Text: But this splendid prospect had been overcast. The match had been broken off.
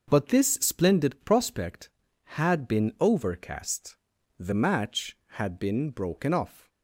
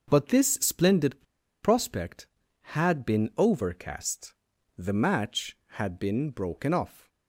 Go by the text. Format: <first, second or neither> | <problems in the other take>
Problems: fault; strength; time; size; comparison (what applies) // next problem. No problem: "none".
first | starts louder than the rest; noticeable; until 1.0 s; 6 dB; noticeable in the first // pauses between "splendid" and "prospect"; at 1.2 s; 0.39 s long